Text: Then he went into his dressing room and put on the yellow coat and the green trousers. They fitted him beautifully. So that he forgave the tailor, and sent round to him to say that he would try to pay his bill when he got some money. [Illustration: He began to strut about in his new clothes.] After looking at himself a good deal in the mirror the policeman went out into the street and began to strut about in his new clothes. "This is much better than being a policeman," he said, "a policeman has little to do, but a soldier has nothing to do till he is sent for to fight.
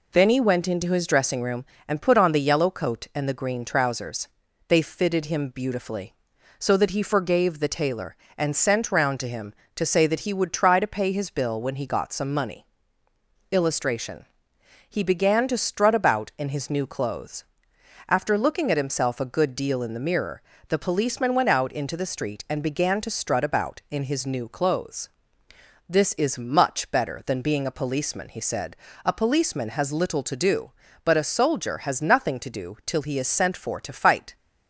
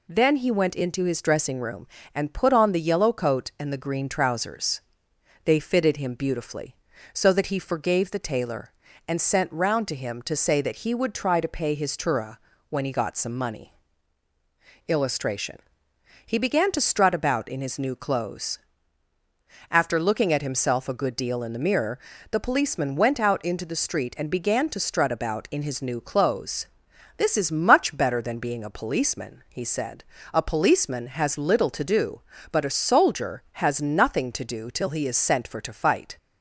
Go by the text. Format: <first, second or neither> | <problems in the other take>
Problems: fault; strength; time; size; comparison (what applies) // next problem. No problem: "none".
first | says "tura" for "bill"; at 11.9 s // pauses between "mirror" and "the"; slight; at 21.9 s; 0.32 s long; slight in the first